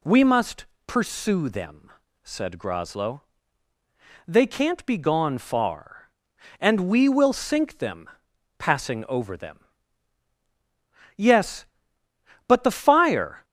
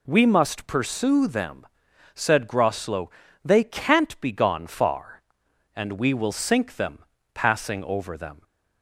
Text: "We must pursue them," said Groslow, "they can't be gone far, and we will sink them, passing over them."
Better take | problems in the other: second | pauses between "must" and "pursue"; slight; at 0.6 s; 0.22 s long // goes on to say "Yes but the fire"; strong; from 11.1 s on; 2.2 s long

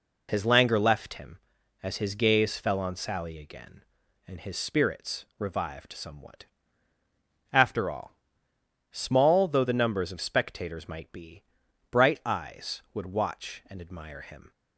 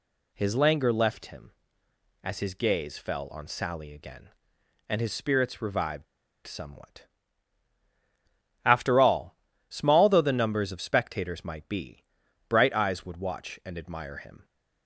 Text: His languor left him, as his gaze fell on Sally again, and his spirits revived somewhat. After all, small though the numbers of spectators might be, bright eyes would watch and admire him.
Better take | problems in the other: first | pauses between "revived" and "somewhat"; at 6.0 s; 0.41 s long

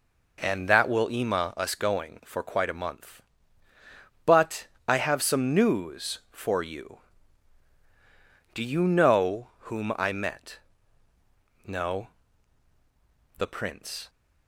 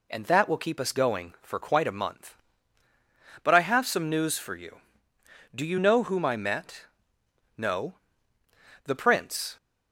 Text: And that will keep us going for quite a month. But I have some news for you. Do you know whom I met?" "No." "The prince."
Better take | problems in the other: second | says "ema" for "keep"; at 1.1 s // pauses between "But" and "I"; slight; at 4.6 s; 0.20 s long

